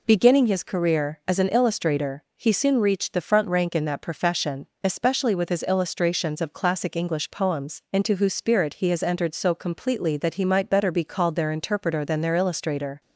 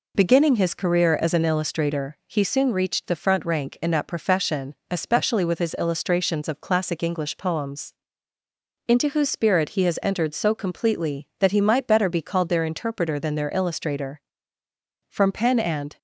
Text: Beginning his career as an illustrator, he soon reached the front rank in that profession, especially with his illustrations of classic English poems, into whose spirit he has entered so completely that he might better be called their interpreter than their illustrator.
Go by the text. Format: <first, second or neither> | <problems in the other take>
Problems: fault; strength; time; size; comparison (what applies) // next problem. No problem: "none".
first | goes on to say "From pen and"; noticeable; from 15.0 s on; 0.88 s long